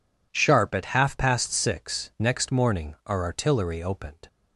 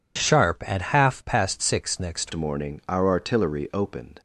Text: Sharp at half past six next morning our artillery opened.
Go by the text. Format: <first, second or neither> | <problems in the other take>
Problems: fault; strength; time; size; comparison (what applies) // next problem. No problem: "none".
first | changes voice at "morning"; from 2.3 s on; 1.9 s long